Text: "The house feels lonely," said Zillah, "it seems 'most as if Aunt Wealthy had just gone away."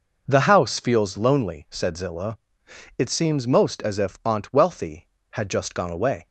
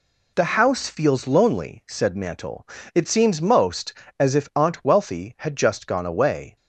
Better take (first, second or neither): first